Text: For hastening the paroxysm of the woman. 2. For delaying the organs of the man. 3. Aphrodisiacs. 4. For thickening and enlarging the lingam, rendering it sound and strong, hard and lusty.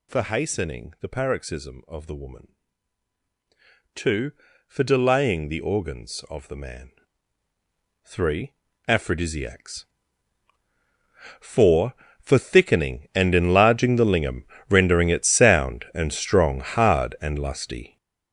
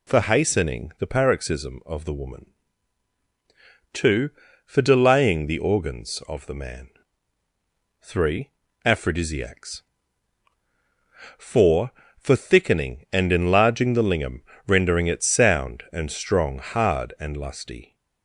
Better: second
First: gets louder; strong; throughout; 10 dB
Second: none

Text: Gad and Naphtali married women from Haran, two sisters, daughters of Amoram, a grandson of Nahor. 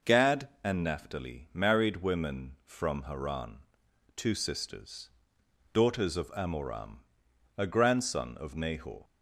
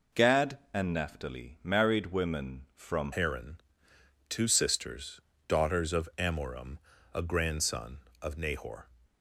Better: first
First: none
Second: changes voice at "Haran"; from 3.1 s on; 5.7 s long

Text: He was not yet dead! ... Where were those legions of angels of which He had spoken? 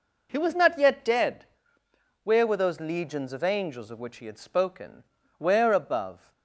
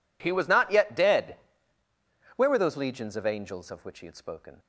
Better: second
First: goes on to say "Where above"; noticeable; from 5.3 s on; 0.94 s long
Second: none

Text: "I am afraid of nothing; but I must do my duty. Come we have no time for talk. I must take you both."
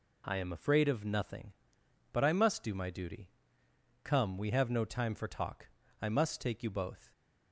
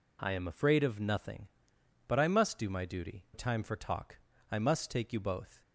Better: first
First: none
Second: skips "Come we have no"; at 3.2 s

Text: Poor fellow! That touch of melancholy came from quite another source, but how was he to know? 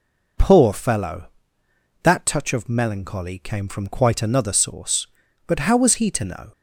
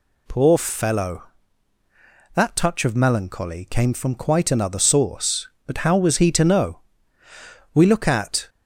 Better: first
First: none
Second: goes on to say "We look at"; noticeable; from 7.7 s on; 0.76 s long

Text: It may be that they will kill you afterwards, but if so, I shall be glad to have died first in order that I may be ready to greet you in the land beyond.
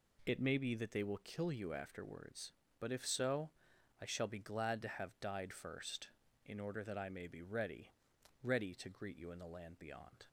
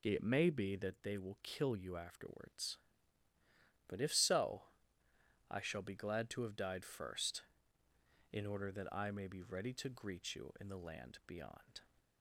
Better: second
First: says "ready" twice; at 8.4 s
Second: none

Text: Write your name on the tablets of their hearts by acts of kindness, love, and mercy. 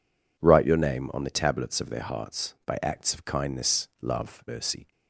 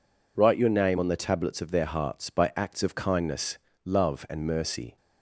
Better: second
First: skips "and"; at 4.4 s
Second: none

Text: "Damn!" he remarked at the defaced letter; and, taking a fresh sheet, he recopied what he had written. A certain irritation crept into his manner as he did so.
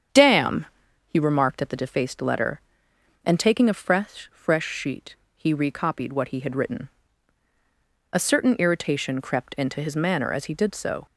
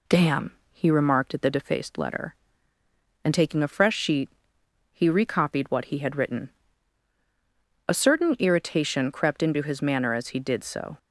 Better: second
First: starts louder than the rest; strong; until 1.5 s; 8 dB // says "fresh" twice; at 4.3 s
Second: none

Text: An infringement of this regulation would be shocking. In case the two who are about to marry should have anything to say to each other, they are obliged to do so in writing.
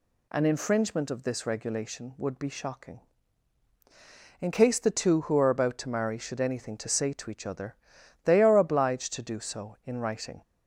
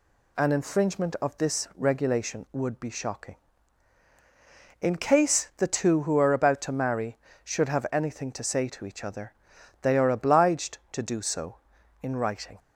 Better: second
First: skips "have"; at 6.4 s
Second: none

